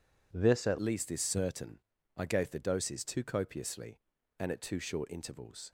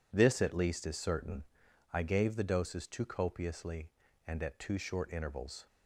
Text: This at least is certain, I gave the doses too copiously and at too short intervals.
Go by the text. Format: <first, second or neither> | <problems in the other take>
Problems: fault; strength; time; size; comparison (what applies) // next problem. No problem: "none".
second | changes voice at "least"; from 0.8 s on; 4.9 s long